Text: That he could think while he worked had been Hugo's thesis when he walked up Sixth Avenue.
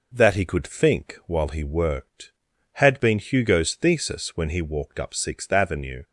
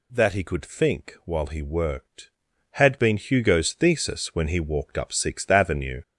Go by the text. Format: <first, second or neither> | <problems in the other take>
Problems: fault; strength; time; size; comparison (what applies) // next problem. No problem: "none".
first | gets louder; throughout; 7 dB